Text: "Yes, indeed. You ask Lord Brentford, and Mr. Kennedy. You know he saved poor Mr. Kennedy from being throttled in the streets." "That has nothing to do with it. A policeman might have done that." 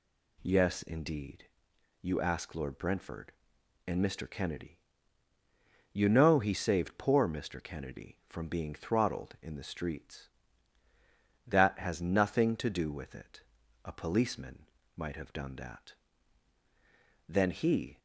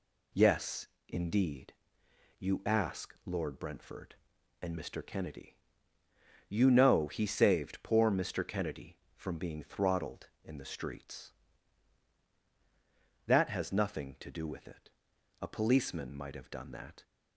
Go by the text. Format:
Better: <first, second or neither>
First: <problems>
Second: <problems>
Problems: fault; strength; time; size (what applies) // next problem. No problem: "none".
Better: second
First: pauses between "policeman" and "might"; slight; at 14.6 s; 0.26 s long // goes on to say "Then he"; noticeable; from 17.2 s on; 0.70 s long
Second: none